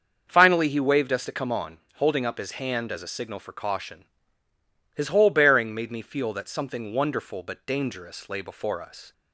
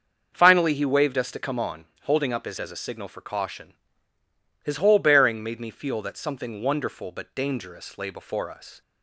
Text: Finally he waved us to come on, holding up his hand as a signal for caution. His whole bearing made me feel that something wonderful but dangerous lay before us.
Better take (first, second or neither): first